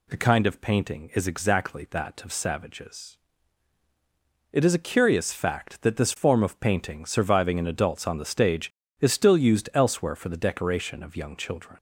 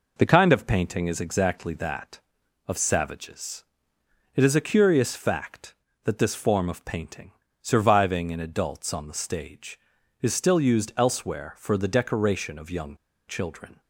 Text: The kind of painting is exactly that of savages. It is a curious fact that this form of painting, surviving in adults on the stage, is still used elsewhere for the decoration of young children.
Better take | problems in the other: first | pauses between "young" and "children"; slight; at 12.9 s; 0.31 s long

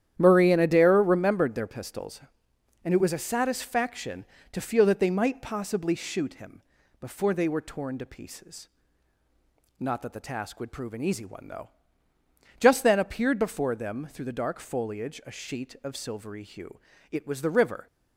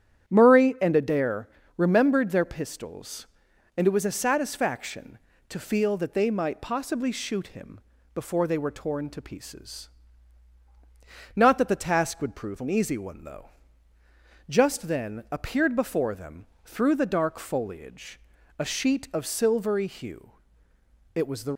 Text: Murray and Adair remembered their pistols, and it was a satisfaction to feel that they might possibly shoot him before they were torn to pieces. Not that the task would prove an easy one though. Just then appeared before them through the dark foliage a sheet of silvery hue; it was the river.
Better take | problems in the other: first | starts louder than the rest; strong; until 1.3 s; 10 dB; strong in the first // pauses between "Adair" and "remembered"; slight; at 1.4 s; 0.28 s long // pauses between "him" and "before"; slight; at 7.7 s; 0.34 s long; also in the first // pauses between "them" and "through"; slight; at 16.4 s; 0.18 s long // pauses between "foliage" and "a"; at 18.1 s; 0.40 s long // stops before "river"; at 21.5 s

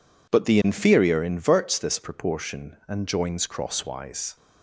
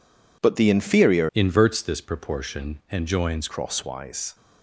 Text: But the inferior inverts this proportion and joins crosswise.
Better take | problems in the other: first | changes voice from "inverts" to "joins"; from 1.3 to 3.4 s; 2.1 s long

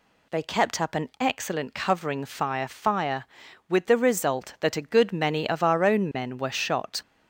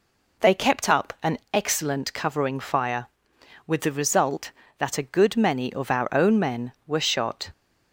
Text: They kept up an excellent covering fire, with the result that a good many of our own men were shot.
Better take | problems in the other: second | says "fire" twice; at 2.6 s

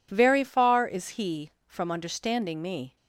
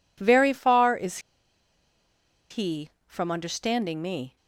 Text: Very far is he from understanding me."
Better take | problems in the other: first | pauses between "is" and "he"; strong; at 1.1 s; 1.3 s long

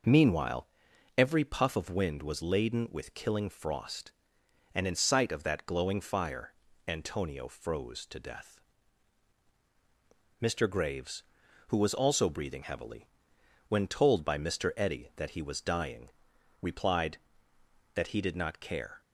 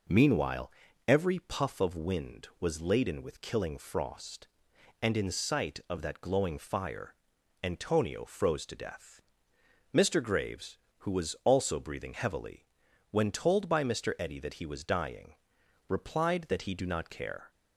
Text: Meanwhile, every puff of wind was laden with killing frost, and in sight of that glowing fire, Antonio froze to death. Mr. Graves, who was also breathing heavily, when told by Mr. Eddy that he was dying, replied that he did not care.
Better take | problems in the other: first | says "do" for "did"; at 16.7 s

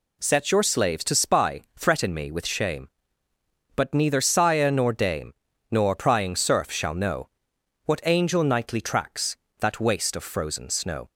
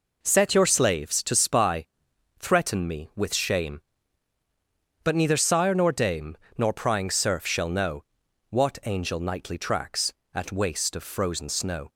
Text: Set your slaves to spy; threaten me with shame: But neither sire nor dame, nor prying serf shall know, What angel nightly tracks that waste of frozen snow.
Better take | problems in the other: first | says "at" for "that"; at 10.3 s

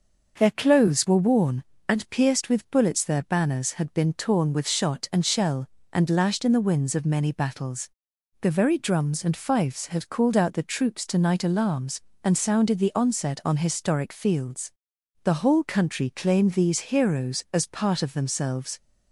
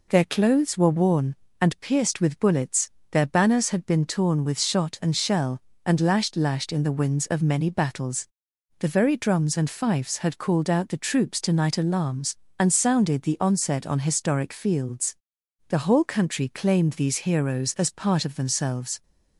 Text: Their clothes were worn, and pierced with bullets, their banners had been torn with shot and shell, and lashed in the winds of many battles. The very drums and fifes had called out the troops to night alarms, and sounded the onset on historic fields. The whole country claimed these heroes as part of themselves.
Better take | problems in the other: first | says "lashed" twice; at 6.3 s

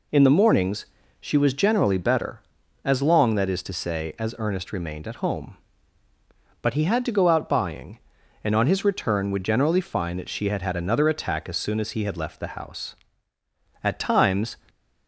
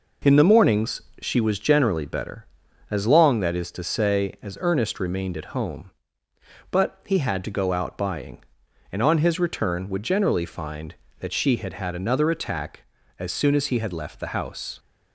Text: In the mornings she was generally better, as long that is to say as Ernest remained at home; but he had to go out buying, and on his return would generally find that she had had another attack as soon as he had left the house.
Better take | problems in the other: second | pauses between "mornings" and "she"; slight; at 0.8 s; 0.34 s long; slight in the second // goes on to say "At times"; noticeable; from 13.8 s on; 0.72 s long

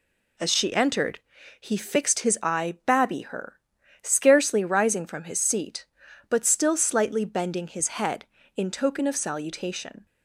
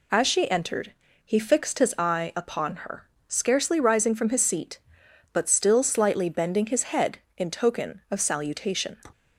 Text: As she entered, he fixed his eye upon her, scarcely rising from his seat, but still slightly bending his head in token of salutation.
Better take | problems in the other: second | says "babby" for "upon"; at 2.8 s

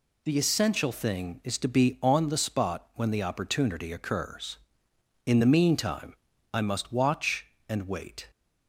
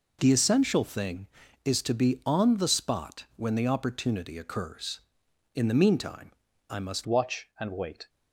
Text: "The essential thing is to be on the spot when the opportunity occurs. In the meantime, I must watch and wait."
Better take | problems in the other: first | changes voice at "watch"; from 7.0 s on; 1.0 s long

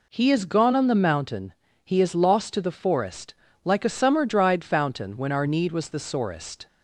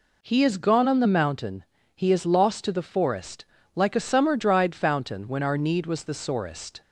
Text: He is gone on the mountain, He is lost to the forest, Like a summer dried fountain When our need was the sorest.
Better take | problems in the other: neither | none

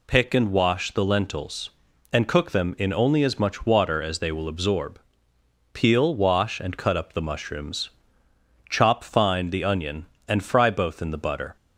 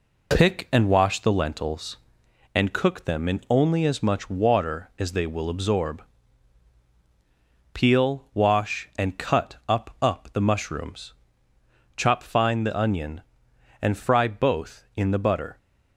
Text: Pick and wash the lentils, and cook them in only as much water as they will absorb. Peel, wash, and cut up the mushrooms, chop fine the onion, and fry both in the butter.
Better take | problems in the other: first | says "up" twice; at 9.9 s

